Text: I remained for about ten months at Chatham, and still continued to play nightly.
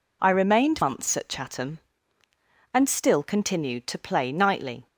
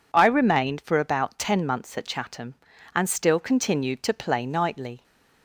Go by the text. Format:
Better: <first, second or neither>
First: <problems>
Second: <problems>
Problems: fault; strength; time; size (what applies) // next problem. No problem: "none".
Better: second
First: skips "for about ten"; at 0.8 s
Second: none